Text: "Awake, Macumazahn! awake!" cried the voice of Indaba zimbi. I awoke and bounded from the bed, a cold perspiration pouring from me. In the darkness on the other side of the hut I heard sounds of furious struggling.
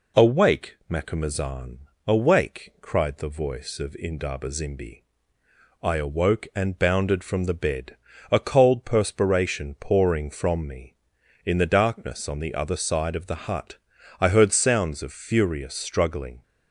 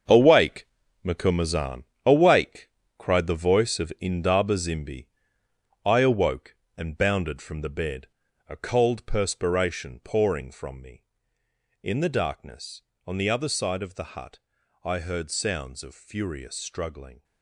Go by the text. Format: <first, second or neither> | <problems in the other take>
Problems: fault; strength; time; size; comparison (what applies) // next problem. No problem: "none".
first | gets quieter; strong; throughout; 10 dB // pauses between "hut" and "I"; noticeable; at 14.3 s; 0.46 s long; also in the first